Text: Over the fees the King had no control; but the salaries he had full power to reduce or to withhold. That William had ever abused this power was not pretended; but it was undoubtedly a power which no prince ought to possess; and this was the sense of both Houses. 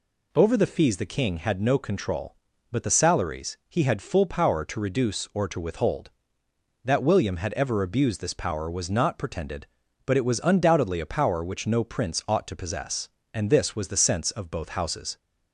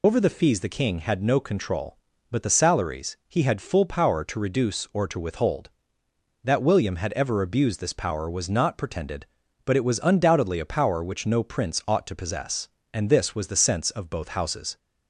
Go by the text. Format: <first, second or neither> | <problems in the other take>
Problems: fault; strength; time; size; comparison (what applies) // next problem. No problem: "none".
first | loses the start of "Over"; at 0.0 s; 85 ms